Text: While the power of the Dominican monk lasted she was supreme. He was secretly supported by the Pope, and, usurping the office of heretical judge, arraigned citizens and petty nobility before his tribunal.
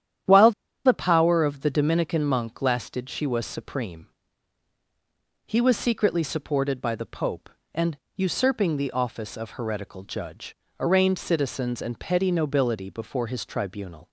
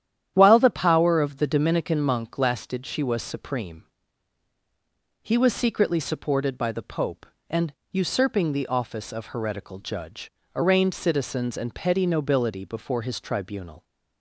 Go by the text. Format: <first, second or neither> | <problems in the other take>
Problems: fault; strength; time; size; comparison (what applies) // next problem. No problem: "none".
second | starts louder than the rest; strong; until 1.6 s; 10.5 dB; strong in the second // pauses between "While" and "the"; slight; at 0.5 s; 0.34 s long